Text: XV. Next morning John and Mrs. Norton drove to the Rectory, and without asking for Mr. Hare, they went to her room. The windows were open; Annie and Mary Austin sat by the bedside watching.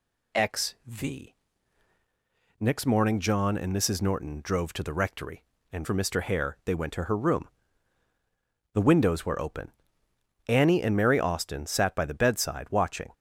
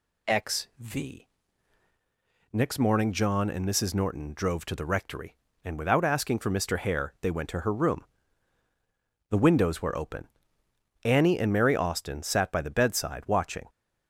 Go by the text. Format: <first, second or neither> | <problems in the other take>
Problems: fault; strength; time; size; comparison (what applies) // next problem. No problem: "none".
second | skips "without asking"; at 5.8 s